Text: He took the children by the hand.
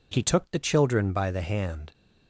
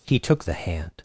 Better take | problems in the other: first | skips "the children by"; at 0.4 s

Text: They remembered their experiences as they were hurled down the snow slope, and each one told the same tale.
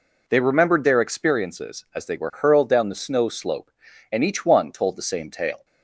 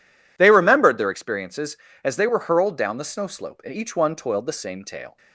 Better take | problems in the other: first | says "toiled" for "told"; at 4.1 s

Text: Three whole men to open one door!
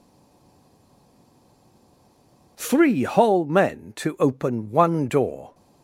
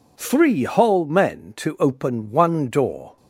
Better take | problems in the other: second | stays silent before the first word; strong; until 2.5 s; 2.5 s long

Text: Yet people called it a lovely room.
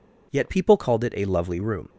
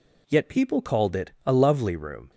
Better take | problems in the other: neither | none

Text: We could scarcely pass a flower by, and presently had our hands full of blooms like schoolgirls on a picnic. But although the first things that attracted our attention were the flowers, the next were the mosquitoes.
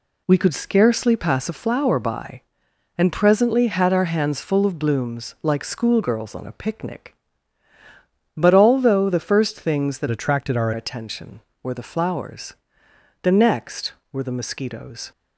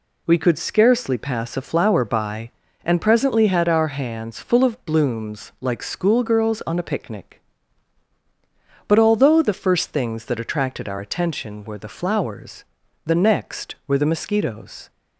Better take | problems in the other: second | changes voice from "attracted" to "our"; from 10.0 to 10.7 s; 0.7 s long

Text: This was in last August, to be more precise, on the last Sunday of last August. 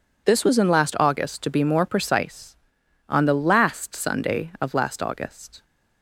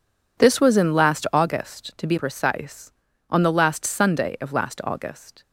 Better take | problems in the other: first | skips "more"; at 2.1 s

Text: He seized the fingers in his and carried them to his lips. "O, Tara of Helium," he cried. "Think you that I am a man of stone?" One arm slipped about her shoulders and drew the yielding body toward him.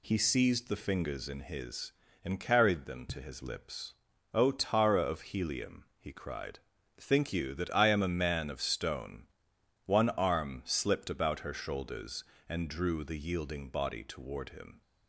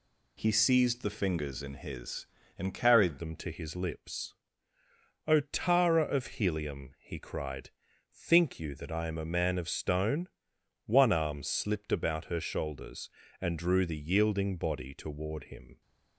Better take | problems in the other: first | changes voice at "them"; from 3.1 s on; 12.7 s long

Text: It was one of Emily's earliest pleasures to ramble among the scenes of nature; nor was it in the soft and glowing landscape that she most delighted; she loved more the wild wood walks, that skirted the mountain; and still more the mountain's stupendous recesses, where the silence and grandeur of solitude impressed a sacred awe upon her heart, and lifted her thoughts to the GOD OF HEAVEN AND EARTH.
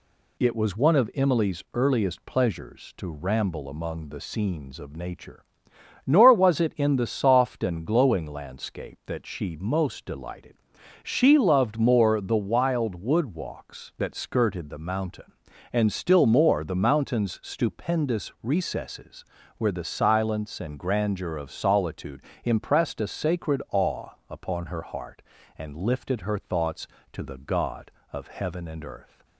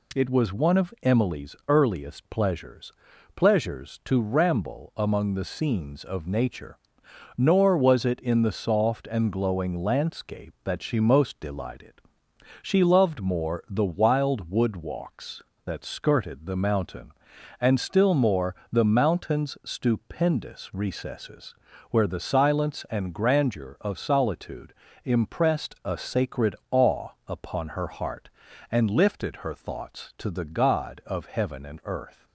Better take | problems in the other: first | says "pleasures" twice; at 3.3 s // pauses between "more" and "the"; slight; at 18.5 s; 0.16 s long // pauses between "solitude" and "impressed"; slight; at 24.7 s; 0.32 s long; slight in the first // pauses between "sacred" and "awe"; slight; at 26.5 s; 0.16 s long // pauses between "awe" and "upon"; slight; at 27.0 s; 0.18 s long; slight in the first

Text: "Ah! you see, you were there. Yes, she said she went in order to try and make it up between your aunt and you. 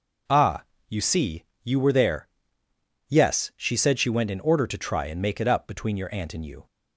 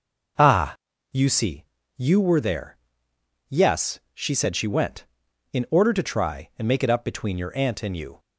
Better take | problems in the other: neither | none

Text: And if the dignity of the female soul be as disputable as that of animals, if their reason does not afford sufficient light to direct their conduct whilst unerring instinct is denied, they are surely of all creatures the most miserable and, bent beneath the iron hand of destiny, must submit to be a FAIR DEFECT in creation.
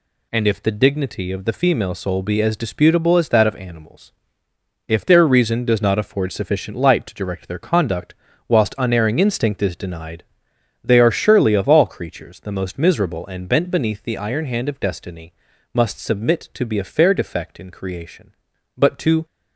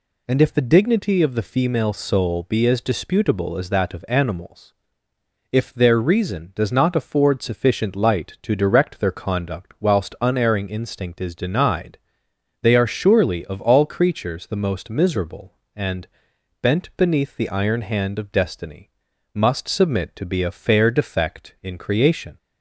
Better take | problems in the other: second | pauses between "conduct" and "whilst"; slight; at 8.1 s; 0.34 s long // goes on to say "But to"; slight; from 18.7 s on; 0.48 s long

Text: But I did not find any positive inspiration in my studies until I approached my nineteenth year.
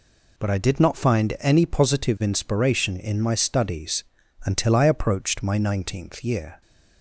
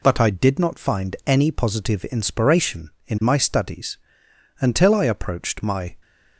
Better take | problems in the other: first | pauses between "studies" and "until"; noticeable; at 3.9 s; 0.62 s long; also in the first // stops before "nineteenth year"; at 6.0 s

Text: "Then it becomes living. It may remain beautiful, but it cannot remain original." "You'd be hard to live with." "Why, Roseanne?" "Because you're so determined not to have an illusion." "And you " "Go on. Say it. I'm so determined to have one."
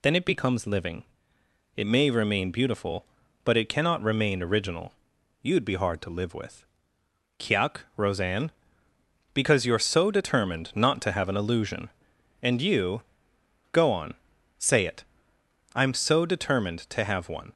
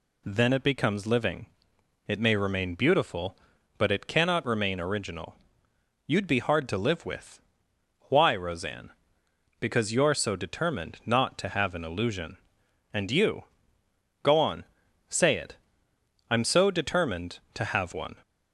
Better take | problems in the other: second | says "Kiak" for "Why"; at 7.3 s

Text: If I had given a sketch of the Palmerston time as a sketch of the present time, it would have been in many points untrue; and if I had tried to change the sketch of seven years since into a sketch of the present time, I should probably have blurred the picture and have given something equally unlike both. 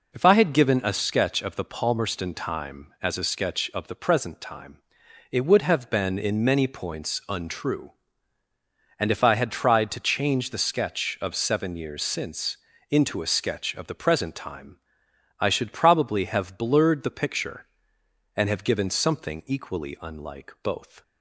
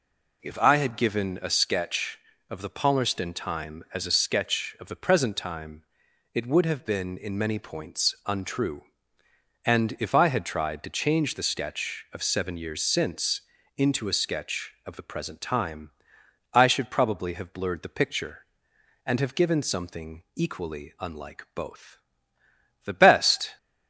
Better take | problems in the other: first | pauses between "since" and "into"; slight; at 13.4 s; 0.36 s long; slight in the first // goes on to say "The best"; noticeable; from 22.8 s on; 0.72 s long

